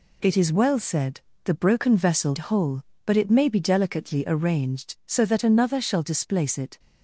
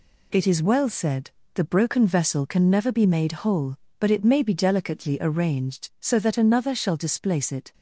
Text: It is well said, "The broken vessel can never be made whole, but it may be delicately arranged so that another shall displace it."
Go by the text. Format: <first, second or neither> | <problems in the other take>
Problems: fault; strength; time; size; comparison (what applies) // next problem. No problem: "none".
second | skips "can never be made"; at 2.3 s